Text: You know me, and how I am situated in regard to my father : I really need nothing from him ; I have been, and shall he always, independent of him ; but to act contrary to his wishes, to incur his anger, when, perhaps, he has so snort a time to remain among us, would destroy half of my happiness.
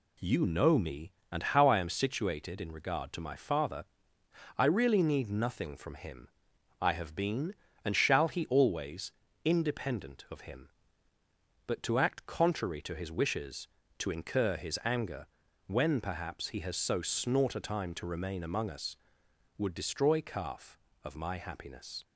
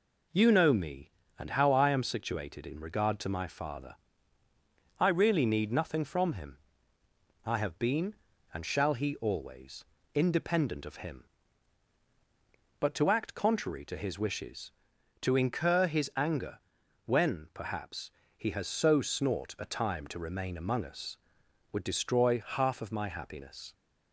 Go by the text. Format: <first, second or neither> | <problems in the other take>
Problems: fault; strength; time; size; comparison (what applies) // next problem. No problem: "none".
second | says "calf" for "half"; at 20.2 s